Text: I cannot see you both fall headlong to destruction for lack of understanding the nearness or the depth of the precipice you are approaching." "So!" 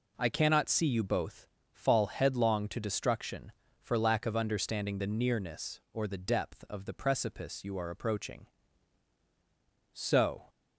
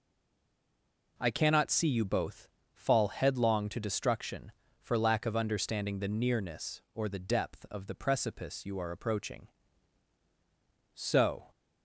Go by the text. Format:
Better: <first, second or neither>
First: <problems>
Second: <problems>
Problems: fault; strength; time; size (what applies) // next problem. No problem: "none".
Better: first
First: pauses between "both" and "fall"; slight; at 1.4 s; 0.26 s long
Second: stays silent before the first word; noticeable; until 1.1 s; 1.1 s long // pauses between "both" and "fall"; slight; at 2.4 s; 0.26 s long